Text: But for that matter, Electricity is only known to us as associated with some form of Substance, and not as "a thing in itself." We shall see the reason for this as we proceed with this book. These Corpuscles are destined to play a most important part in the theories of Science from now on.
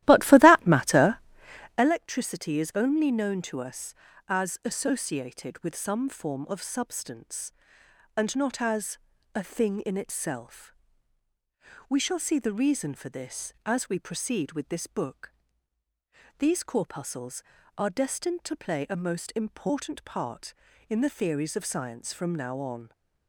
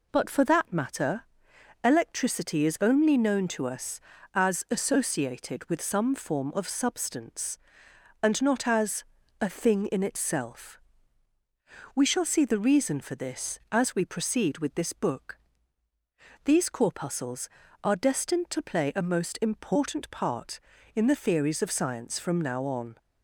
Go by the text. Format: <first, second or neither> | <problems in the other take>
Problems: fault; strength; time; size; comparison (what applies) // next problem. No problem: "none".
second | starts louder than the rest; strong; until 1.9 s; 15 dB // pauses between "as" and "a"; slight; at 8.9 s; 0.36 s long; slight in the second